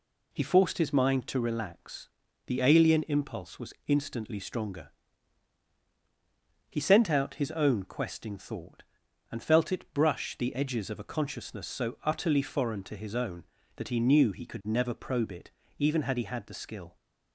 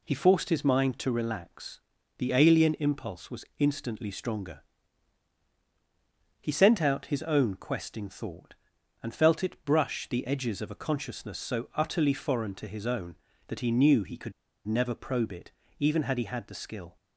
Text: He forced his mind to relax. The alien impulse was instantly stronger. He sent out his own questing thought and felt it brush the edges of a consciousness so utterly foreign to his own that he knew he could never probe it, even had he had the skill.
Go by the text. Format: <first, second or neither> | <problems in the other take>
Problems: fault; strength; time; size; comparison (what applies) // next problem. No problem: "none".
first | pauses between "could" and "never"; slight; at 14.3 s; 0.33 s long